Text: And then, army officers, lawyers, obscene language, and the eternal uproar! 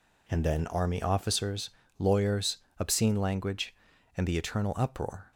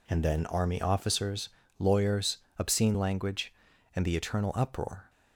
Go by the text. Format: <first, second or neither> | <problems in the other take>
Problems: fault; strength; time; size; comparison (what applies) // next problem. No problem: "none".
neither | none